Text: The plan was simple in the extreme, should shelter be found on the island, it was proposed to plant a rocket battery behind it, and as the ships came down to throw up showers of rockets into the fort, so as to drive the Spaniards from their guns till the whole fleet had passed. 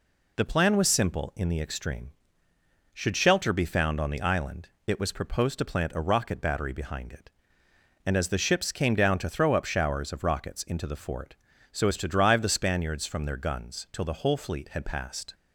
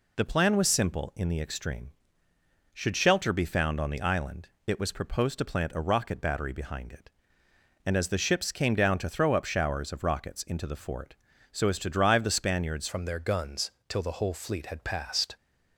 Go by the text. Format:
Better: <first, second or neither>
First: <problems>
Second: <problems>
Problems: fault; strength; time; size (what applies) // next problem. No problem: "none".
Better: first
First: none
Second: changes voice at "from"; from 12.8 s on; 2.5 s long // pauses between "guns" and "till"; slight; at 13.7 s; 0.18 s long